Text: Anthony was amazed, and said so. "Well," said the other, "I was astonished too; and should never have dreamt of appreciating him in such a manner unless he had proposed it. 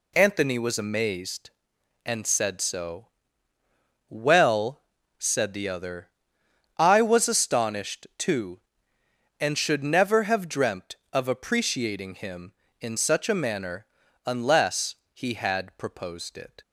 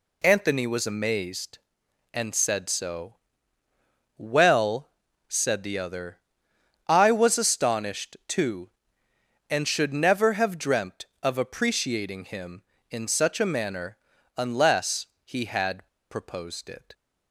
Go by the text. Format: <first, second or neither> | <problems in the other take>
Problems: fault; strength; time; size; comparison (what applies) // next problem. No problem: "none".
first | pauses between "manner" and "unless"; at 13.9 s; 0.40 s long; also in the first // pauses between "unless" and "he"; slight; at 15.0 s; 0.18 s long; slight in the first // pauses between "had" and "proposed"; slight; at 15.8 s; 0.23 s long